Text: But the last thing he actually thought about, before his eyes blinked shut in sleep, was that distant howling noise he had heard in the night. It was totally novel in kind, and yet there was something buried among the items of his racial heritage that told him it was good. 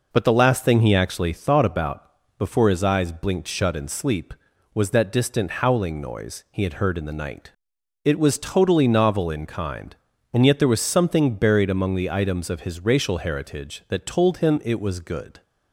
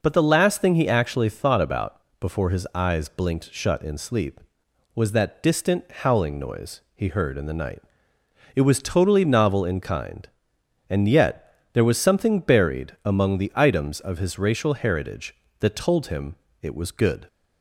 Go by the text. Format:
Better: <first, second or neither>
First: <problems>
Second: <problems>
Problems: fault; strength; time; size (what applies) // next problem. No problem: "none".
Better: first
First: none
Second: skips "had"; at 7.0 s // pauses between "yet" and "there"; slight; at 11.5 s; 0.20 s long // pauses between "him" and "it"; slight; at 16.3 s; 0.26 s long